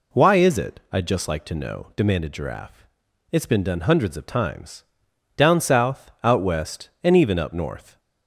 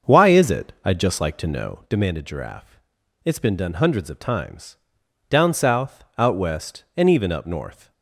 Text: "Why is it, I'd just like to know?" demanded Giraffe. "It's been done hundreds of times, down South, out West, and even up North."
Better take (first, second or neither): first